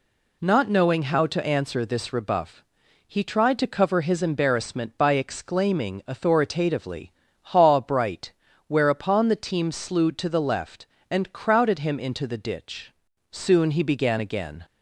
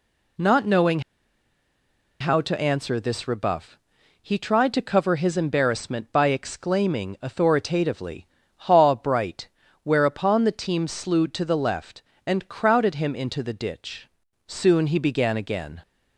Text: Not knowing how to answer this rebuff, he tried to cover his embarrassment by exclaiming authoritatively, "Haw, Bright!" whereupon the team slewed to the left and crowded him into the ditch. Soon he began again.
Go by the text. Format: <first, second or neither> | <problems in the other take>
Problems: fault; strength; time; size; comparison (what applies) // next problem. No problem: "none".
first | pauses between "knowing" and "how"; at 0.9 s; 1.2 s long